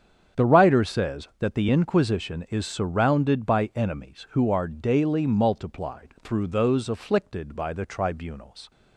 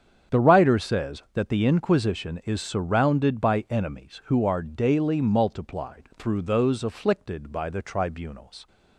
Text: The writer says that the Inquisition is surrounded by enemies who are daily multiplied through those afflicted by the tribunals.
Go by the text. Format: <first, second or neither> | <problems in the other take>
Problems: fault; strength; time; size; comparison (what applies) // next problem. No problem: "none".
neither | starts louder than the rest; strong; the same in both